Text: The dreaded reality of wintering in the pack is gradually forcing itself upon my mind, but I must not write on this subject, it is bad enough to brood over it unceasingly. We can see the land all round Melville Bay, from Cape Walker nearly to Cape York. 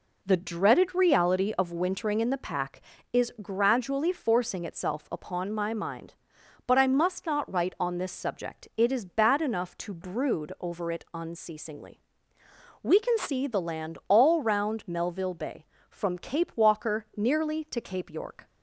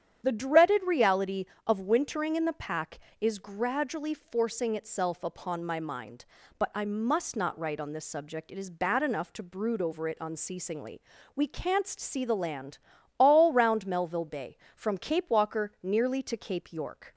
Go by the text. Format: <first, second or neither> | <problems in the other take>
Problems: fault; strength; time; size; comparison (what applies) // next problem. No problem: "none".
first | starts louder than the rest; strong; until 1.2 s; 9 dB // says "canst" for "can"; at 11.4 s // pauses between "land" and "all"; at 12.7 s; 0.42 s long